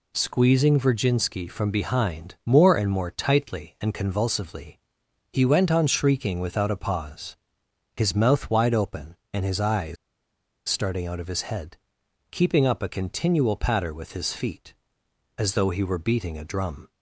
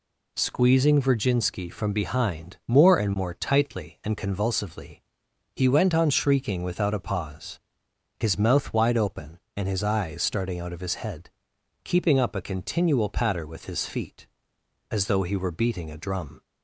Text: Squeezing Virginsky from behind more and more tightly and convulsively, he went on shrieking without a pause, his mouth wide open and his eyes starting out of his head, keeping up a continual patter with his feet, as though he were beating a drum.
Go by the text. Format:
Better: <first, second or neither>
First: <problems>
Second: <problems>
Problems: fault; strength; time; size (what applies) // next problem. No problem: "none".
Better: second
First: pauses between "eyes" and "starting"; noticeable; at 9.9 s; 0.72 s long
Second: none